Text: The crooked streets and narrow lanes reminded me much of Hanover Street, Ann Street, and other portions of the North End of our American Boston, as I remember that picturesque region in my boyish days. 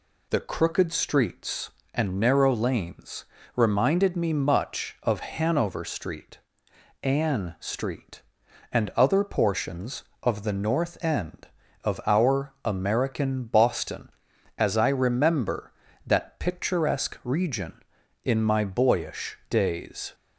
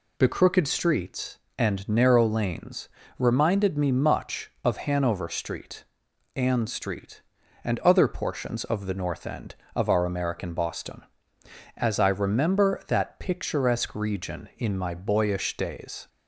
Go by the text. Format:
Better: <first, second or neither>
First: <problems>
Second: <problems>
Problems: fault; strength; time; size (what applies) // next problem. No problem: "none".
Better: neither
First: pauses between "lanes" and "reminded"; slight; at 3.2 s; 0.28 s long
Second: pauses between "lanes" and "reminded"; slight; at 2.8 s; 0.30 s long